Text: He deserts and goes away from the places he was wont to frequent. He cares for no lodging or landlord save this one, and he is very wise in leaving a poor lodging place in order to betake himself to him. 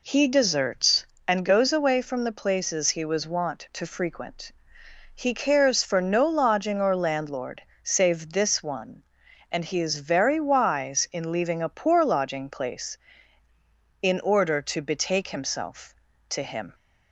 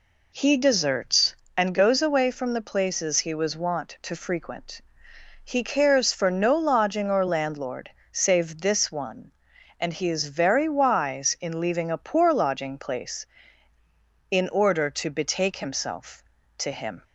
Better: neither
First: pauses between "landlord" and "save"; slight; at 7.6 s; 0.21 s long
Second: pauses between "landlord" and "save"; slight; at 7.9 s; 0.22 s long

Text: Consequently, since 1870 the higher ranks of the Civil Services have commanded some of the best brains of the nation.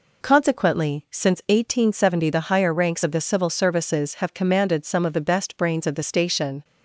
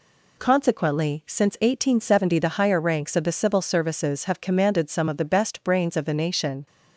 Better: second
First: says "station" for "nation"; at 6.0 s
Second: none

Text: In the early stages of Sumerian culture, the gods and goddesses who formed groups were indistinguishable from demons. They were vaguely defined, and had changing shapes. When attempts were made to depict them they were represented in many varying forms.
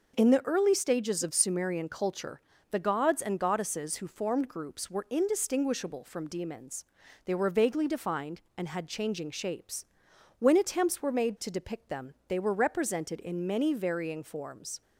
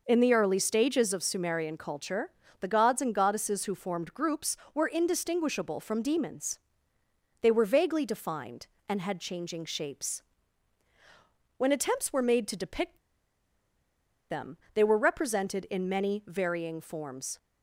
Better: first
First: none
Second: pauses between "depict" and "them"; strong; at 12.9 s; 1.3 s long // pauses between "them" and "they"; slight; at 14.5 s; 0.18 s long

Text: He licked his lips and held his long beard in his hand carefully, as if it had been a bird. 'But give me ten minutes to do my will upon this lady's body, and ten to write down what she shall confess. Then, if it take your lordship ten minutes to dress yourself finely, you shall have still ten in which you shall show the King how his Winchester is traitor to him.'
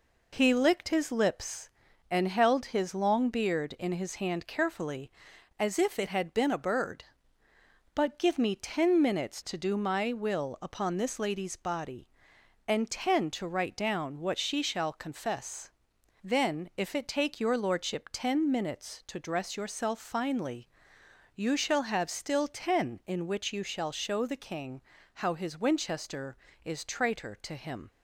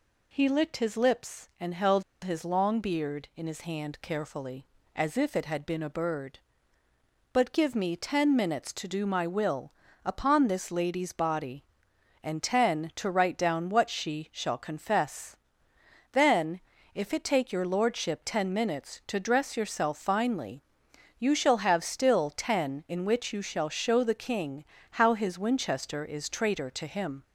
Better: first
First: pauses between "King" and "how"; slight; at 24.8 s; 0.32 s long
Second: pauses between "held" and "his"; slight; at 2.0 s; 0.21 s long // pauses between "will" and "upon"; slight; at 9.7 s; 0.34 s long // pauses between "King" and "how"; slight; at 24.6 s; 0.34 s long

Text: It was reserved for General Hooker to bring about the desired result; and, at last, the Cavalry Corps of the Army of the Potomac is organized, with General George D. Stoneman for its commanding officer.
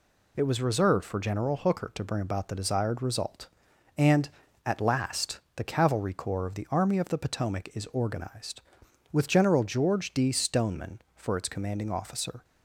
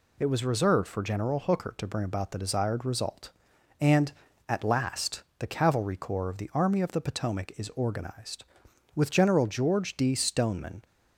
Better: first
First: none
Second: stops before "for its commanding officer"; at 10.8 s

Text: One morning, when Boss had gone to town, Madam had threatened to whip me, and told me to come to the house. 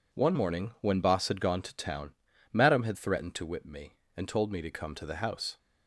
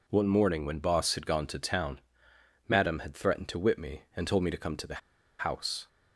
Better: first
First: none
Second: pauses between "the" and "house"; at 5.0 s; 0.41 s long

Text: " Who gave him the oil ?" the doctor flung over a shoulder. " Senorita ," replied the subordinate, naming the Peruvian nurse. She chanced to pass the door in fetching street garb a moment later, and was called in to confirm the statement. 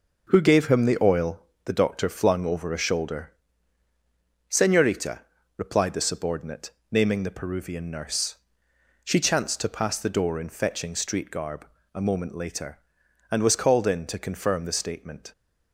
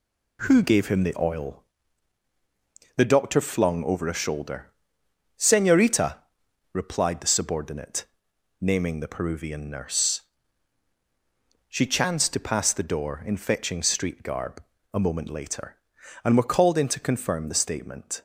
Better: first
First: pauses between "garb" and "a"; slight; at 11.6 s; 0.28 s long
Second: pauses between "garb" and "a"; slight; at 14.6 s; 0.30 s long // says "were" for "was"; at 16.3 s

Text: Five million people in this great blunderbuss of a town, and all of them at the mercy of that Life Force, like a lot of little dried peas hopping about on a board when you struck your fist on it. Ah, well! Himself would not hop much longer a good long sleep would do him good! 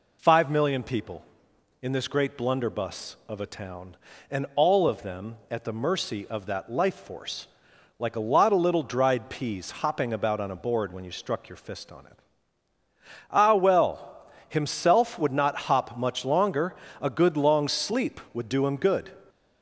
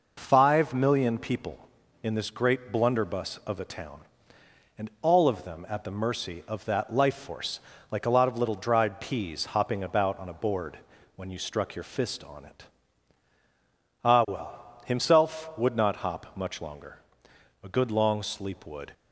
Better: first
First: pauses between "longer" and "a"; slight; at 16.7 s; 0.28 s long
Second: pauses between "board" and "when"; at 10.7 s; 0.40 s long // pauses between "longer" and "a"; noticeable; at 16.9 s; 0.64 s long // stops before "do him good"; at 18.9 s

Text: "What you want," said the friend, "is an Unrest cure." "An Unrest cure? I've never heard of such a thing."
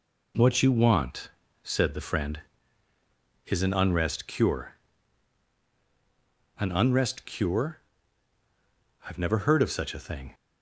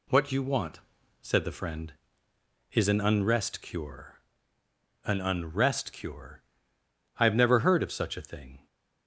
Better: neither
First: none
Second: none

